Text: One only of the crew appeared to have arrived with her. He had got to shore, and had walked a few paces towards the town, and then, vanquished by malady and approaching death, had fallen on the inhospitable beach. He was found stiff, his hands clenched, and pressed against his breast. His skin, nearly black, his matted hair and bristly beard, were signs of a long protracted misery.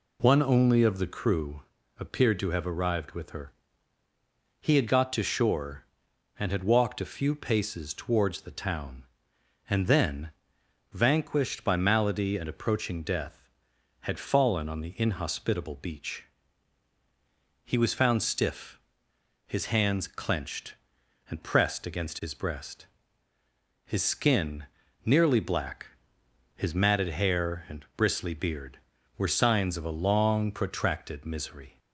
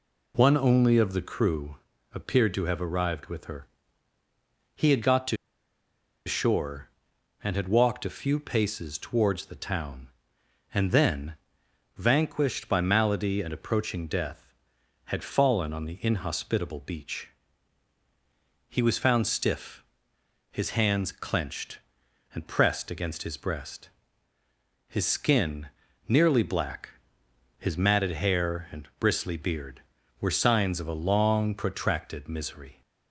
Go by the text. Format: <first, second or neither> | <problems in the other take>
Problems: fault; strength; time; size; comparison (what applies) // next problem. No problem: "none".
first | pauses between "crew" and "appeared"; slight; at 1.7 s; 0.36 s long; slight in the first // pauses between "to" and "shore"; noticeable; at 5.3 s; 0.90 s long